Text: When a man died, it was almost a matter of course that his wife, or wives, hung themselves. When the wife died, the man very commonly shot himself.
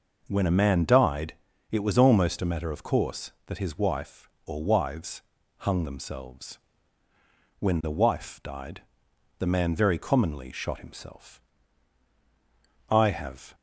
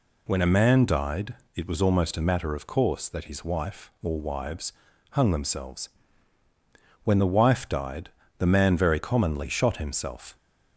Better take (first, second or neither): second